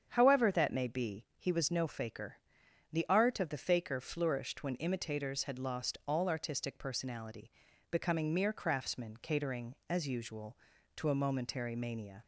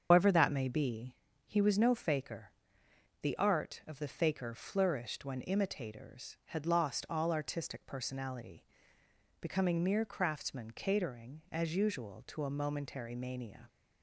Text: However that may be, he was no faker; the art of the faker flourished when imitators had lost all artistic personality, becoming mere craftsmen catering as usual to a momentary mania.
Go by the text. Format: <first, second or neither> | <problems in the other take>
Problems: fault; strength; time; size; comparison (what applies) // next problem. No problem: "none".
first | loses the start of "However"; at 0.1 s; 135 ms // starts louder than the rest; until 1.1 s; 7 dB; strong in the first